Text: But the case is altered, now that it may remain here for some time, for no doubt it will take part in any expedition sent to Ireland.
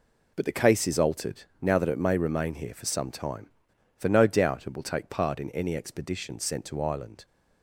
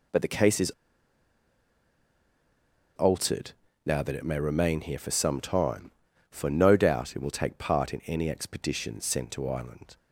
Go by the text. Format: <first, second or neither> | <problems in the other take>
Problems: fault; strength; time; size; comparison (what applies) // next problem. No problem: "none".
first | pauses between "is" and "altered"; strong; at 0.7 s; 2.2 s long